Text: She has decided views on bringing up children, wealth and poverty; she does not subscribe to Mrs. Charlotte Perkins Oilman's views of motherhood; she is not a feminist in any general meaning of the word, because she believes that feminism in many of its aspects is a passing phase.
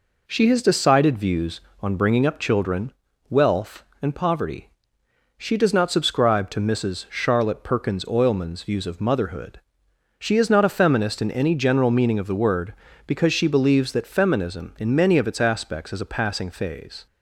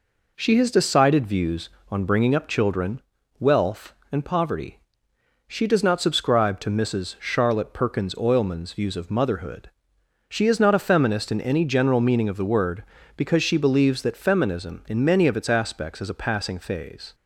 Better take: neither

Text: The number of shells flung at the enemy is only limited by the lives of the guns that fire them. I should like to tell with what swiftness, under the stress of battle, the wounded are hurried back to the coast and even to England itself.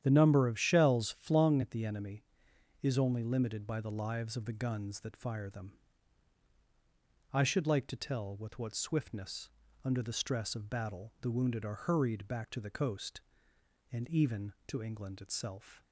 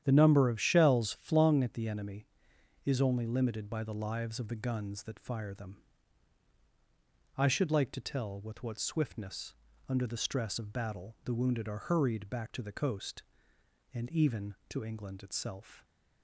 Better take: neither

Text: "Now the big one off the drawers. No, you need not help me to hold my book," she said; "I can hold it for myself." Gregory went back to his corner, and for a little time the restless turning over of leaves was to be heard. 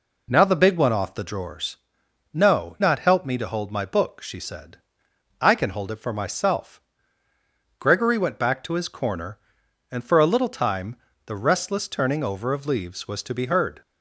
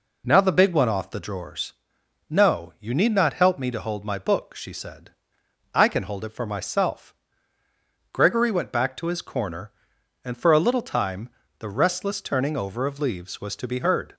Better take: second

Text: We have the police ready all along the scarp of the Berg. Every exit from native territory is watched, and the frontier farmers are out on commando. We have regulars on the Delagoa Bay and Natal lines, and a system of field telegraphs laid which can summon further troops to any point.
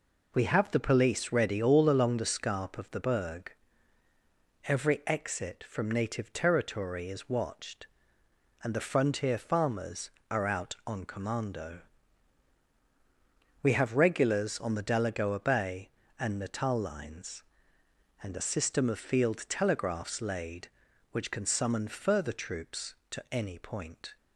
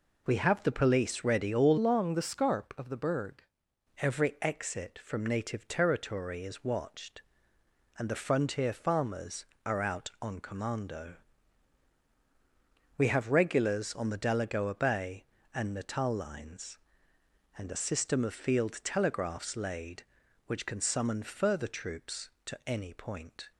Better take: first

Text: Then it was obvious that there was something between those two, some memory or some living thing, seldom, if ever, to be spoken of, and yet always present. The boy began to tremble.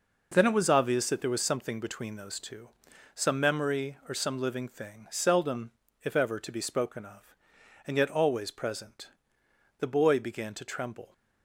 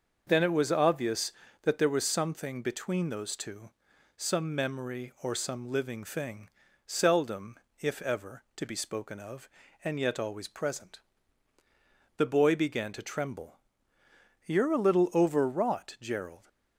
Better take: first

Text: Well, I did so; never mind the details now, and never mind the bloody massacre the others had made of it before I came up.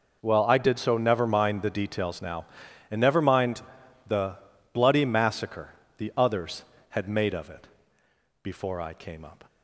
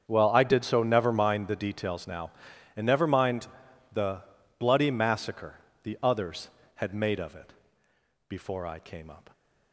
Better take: first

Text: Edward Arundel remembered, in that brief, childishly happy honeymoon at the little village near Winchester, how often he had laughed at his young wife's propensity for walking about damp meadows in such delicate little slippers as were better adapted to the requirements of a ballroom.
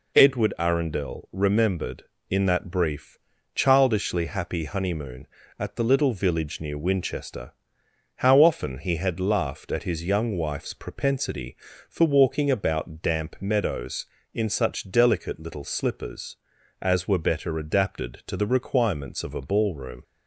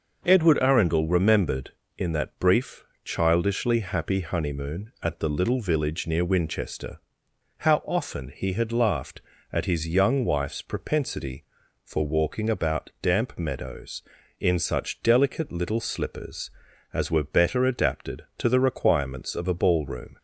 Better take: neither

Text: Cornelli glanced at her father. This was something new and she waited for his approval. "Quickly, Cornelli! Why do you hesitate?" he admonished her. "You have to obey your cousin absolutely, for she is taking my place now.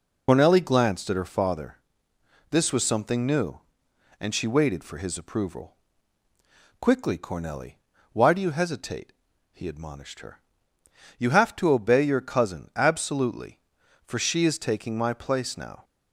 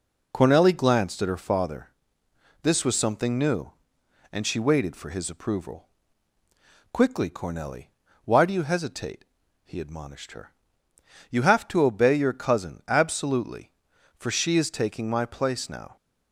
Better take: second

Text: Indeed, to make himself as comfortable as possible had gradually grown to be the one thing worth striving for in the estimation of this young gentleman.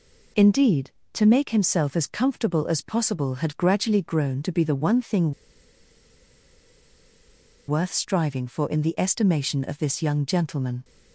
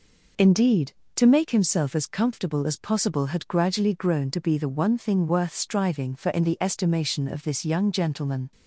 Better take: second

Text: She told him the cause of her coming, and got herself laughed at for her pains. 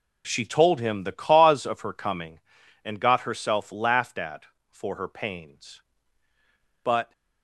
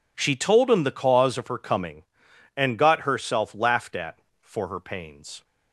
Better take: second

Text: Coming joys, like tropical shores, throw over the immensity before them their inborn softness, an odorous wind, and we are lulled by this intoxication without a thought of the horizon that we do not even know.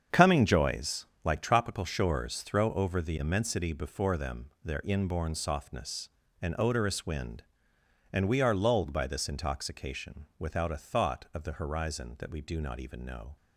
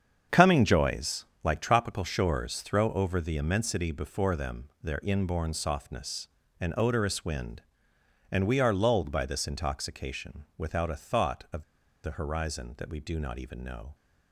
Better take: first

